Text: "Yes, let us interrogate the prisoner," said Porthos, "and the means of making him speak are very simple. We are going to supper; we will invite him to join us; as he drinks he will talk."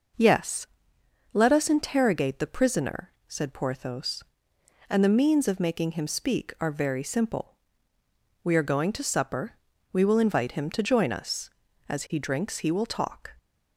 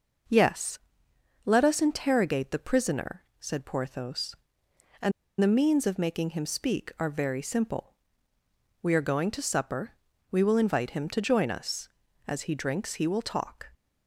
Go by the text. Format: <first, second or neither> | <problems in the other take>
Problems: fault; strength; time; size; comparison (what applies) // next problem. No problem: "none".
first | pauses between "and" and "the"; slight; at 5.1 s; 0.29 s long